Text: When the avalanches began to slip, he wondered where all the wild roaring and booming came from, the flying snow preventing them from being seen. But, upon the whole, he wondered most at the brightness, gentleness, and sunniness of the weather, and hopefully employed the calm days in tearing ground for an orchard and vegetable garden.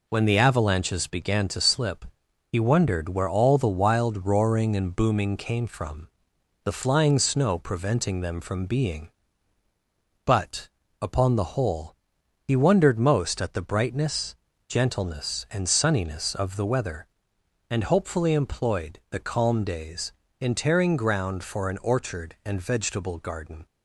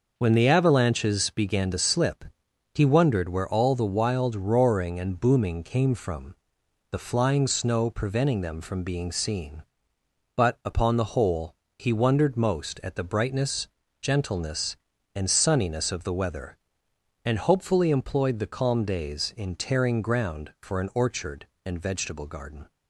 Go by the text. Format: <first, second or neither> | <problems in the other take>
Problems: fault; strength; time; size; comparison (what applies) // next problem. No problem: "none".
second | skips "seen"; at 9.6 s